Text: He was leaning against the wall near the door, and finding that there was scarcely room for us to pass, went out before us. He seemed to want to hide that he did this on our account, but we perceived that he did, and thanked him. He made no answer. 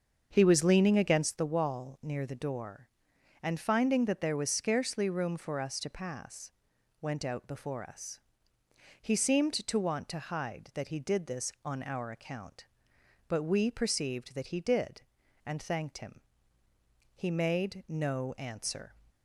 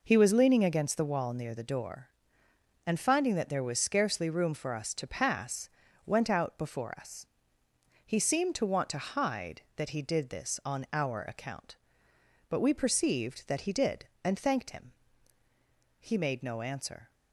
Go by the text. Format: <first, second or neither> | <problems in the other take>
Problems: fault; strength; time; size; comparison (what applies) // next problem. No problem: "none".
second | starts louder than the rest; until 1.4 s; 7 dB